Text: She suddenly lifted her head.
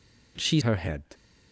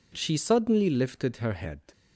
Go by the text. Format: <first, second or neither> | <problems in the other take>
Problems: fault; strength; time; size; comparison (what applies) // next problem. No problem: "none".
second | skips "suddenly lifted"; at 0.6 s